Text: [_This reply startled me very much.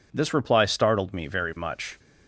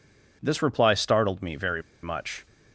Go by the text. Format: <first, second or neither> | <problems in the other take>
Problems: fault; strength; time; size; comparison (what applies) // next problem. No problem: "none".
first | pauses between "very" and "much"; slight; at 1.8 s; 0.21 s long